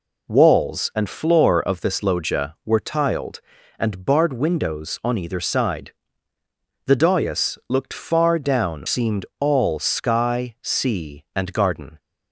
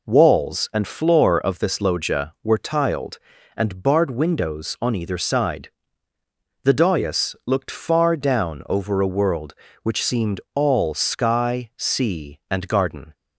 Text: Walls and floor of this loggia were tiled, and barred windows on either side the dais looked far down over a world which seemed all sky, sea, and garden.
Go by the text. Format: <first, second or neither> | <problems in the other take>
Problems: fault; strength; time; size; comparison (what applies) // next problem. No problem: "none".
second | pauses between "side" and "the"; noticeable; at 5.9 s; 0.94 s long; noticeable in the second // skips "over a world which"; at 8.8 s